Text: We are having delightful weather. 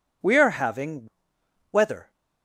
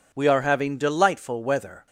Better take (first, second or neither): second